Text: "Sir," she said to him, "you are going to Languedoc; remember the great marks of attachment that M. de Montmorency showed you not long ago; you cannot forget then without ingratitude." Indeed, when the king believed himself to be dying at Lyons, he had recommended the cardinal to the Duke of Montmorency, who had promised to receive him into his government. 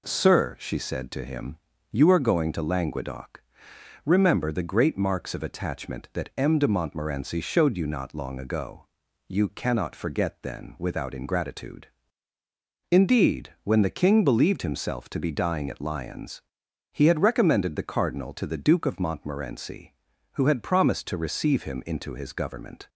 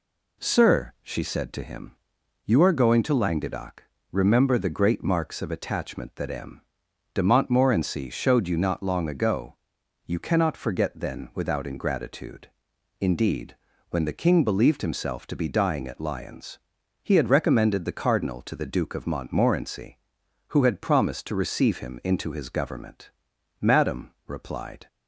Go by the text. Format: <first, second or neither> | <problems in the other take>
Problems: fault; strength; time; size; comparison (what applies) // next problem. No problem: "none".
first | goes on to say "Madam replied"; noticeable; from 23.5 s on; 1.2 s long